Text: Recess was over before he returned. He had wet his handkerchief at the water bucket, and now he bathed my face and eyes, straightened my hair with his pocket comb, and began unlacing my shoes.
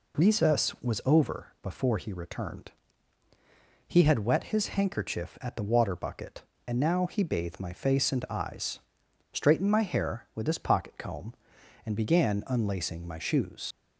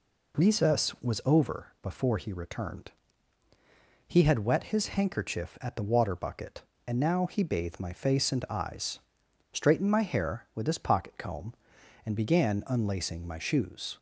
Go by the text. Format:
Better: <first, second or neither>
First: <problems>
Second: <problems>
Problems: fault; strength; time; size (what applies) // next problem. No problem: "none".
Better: second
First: leaves "shoes" unfinished; at 13.7 s; 70 ms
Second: none